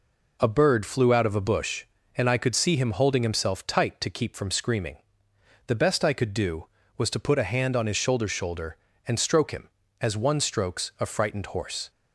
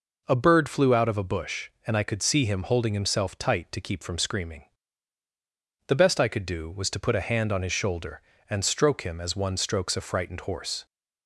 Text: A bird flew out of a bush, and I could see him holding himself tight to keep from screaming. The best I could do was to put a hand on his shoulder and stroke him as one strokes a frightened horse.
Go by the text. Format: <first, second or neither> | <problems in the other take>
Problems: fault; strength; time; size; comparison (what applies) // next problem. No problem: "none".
second | says "shoulder" twice; at 8.2 s